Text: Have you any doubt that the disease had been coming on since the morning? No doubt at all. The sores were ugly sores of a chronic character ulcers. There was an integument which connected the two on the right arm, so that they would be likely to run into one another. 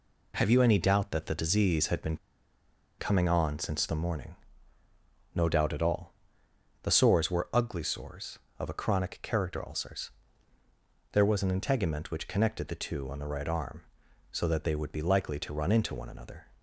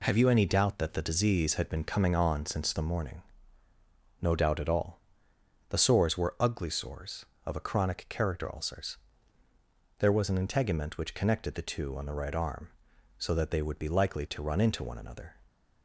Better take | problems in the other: second | pauses between "been" and "coming"; noticeable; at 2.1 s; 0.81 s long

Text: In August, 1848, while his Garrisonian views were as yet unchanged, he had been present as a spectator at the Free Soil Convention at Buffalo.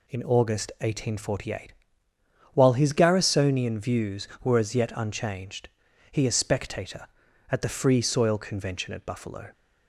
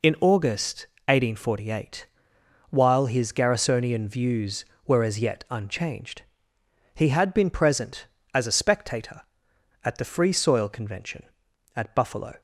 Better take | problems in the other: second | skips "had been present as"; at 6.2 s

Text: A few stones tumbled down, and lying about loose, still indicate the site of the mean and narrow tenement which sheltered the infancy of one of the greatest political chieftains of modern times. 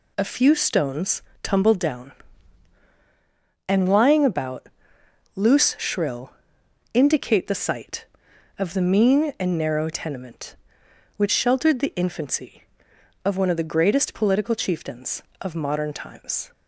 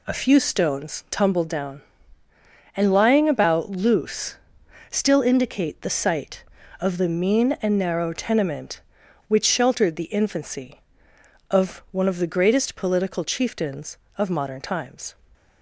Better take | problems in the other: second | pauses between "stones" and "tumbled"; slight; at 1.2 s; 0.18 s long // pauses between "about" and "loose"; noticeable; at 4.6 s; 0.66 s long // says "shrill" for "still"; at 5.7 s

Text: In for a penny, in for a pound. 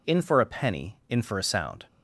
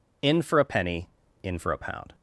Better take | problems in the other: second | says "sound" for "pound"; at 1.4 s

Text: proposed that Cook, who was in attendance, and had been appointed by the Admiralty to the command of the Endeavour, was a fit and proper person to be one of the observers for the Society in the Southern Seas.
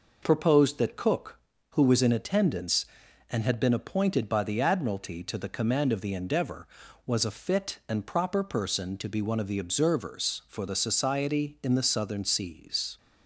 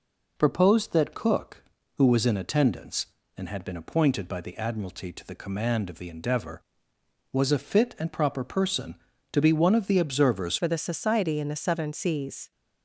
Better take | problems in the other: first | changes voice at "for"; from 10.5 s on; 2.0 s long

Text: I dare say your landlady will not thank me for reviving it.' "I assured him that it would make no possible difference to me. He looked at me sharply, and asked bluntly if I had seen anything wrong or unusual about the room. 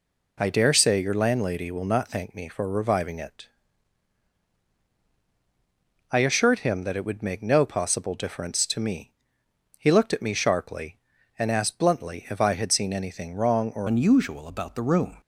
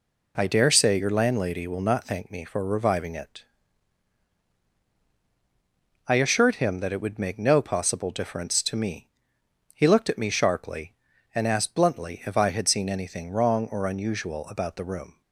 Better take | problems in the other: second | changes voice at "unusual"; from 13.8 s on; 1.3 s long

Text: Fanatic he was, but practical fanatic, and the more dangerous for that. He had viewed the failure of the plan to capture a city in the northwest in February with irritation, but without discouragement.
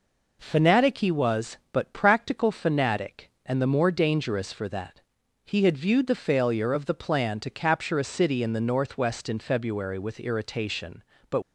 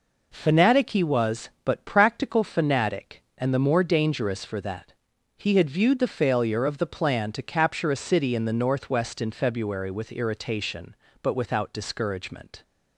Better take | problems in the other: second | stops before "without discouragement"; at 11.4 s

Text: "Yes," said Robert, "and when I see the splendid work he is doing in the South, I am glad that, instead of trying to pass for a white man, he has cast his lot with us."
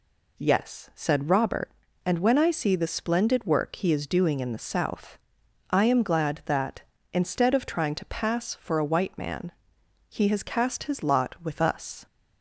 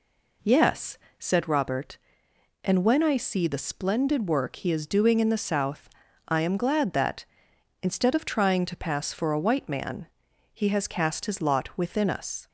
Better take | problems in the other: first | says "within" for "with"; at 11.7 s

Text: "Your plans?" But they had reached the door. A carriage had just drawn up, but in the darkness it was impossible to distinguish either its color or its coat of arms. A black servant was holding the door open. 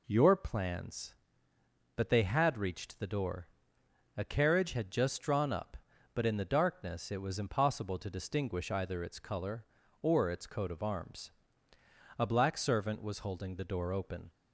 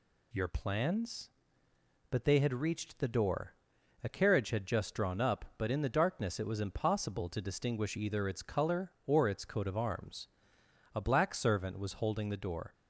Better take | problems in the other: first | stops before "open"; at 12.7 s

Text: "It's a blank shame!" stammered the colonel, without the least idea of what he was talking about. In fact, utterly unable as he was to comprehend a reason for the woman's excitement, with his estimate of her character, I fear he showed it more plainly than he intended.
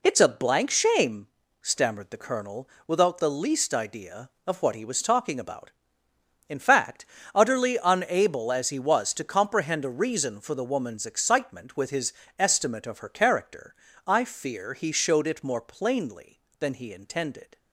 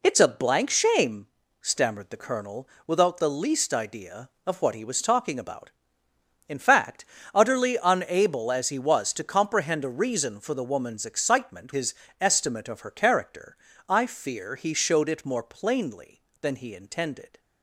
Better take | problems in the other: first | skips "with"; at 11.7 s // pauses between "his" and "estimate"; slight; at 11.9 s; 0.24 s long; slight in the first

